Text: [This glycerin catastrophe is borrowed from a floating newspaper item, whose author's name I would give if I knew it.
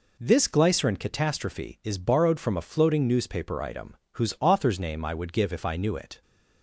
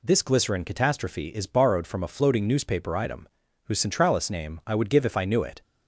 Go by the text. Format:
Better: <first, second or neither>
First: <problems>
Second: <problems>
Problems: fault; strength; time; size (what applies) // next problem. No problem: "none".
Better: first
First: none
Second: says "centralis" for "author's"; at 3.7 s